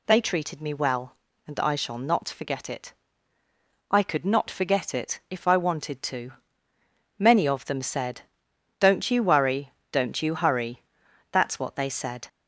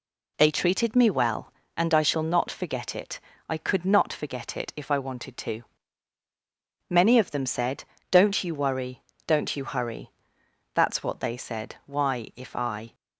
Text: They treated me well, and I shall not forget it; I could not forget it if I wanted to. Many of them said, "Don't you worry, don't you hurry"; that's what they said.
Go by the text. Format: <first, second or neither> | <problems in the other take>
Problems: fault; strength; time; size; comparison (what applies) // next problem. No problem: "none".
first | goes on to say "Why if I"; noticeable; from 11.8 s on; 1.0 s long